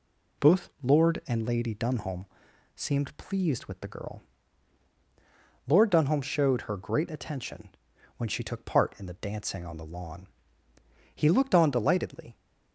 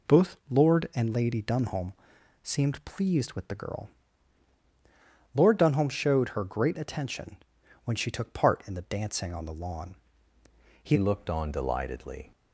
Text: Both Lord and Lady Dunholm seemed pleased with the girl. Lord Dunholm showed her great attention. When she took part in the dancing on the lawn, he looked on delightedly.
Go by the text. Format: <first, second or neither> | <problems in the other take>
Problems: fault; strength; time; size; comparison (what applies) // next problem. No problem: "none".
first | pauses between "Dunholm" and "seemed"; noticeable; at 1.9 s; 0.50 s long; noticeable in the first // changes voice at "looked"; from 10.9 s on; 1.4 s long